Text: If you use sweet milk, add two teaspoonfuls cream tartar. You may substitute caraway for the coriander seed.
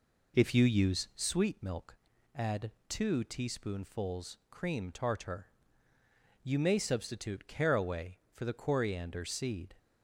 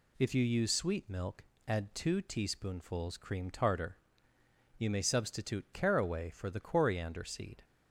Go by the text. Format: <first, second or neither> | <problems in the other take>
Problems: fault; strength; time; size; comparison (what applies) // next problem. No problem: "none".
second | starts louder than the rest; noticeable; until 1.5 s; 4 dB // pauses between "add" and "two"; slight; at 2.7 s; 0.16 s long